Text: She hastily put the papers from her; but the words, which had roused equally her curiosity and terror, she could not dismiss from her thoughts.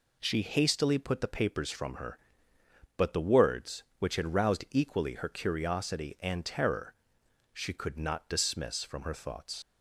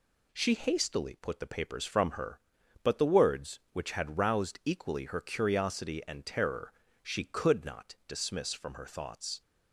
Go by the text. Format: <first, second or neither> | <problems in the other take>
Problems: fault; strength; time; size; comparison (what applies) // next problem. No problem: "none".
second | leaves "thoughts" unfinished; at 9.6 s; 70 ms